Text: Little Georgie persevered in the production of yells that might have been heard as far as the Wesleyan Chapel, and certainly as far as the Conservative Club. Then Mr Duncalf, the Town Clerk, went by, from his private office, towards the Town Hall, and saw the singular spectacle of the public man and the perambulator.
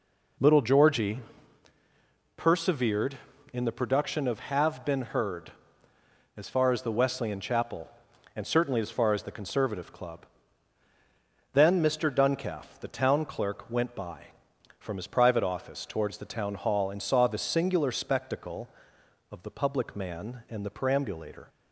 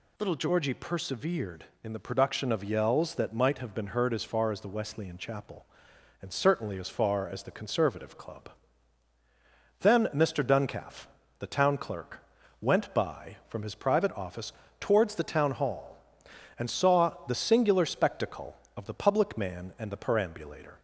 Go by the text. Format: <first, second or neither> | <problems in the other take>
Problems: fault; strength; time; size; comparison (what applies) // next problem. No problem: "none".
second | pauses between "Georgie" and "persevered"; at 1.1 s; 1.1 s long // skips "yells that might"; at 4.3 s